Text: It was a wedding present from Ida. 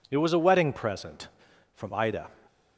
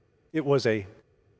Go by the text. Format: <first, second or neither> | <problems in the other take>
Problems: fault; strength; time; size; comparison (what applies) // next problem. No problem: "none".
first | stops before "wedding present from Ida"; at 1.0 s